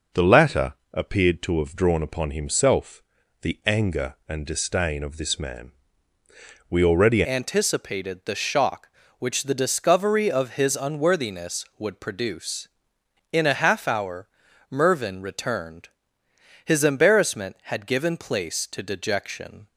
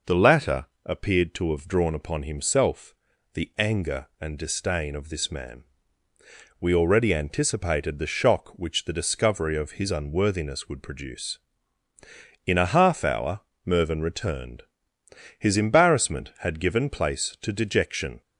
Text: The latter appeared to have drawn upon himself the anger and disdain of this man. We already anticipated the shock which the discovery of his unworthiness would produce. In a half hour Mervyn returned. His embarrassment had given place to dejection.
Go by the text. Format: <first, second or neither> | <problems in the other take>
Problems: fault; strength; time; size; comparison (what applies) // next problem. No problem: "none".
second | pauses between "latter" and "appeared"; slight; at 0.7 s; 0.18 s long; slight in the second // pauses between "himself" and "the"; at 3.0 s; 0.42 s long; also in the second // changes voice at "anticipated"; from 7.2 s on; 12.4 s long // pauses between "hour" and "Mervyn"; at 14.2 s; 0.42 s long; slight in the second